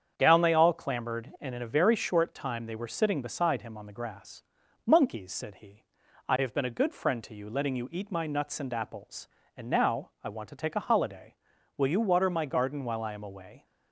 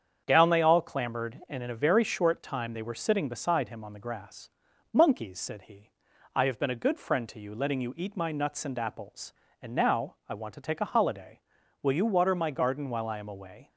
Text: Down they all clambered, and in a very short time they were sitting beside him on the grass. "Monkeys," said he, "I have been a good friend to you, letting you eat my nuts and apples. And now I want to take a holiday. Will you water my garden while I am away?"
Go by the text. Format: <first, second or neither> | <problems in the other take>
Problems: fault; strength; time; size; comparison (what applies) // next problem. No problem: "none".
neither | starts louder than the rest; strong; the same in both